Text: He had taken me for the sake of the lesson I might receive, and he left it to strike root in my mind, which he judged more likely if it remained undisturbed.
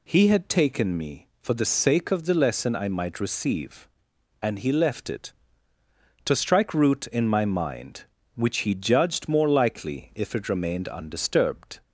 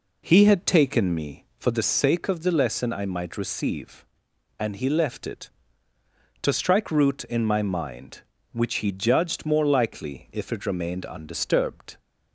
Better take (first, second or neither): first